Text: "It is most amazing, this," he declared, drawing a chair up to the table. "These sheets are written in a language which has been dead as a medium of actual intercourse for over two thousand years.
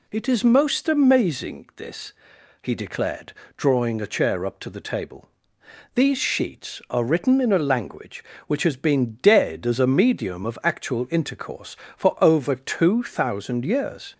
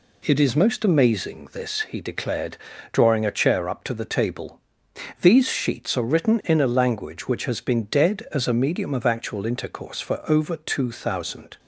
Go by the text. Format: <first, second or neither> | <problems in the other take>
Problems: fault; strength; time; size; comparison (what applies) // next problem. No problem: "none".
first | stops before "years"; at 11.5 s